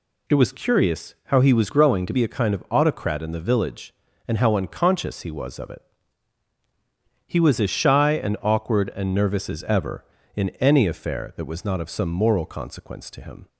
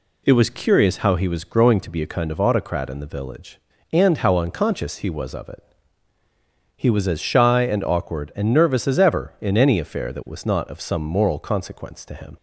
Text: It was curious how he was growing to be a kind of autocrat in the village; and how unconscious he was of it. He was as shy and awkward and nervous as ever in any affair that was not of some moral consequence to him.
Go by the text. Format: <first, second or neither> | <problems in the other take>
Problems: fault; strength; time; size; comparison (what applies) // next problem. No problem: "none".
second | changes voice from "growing" to "to"; from 1.6 to 2.1 s; 0.5 s long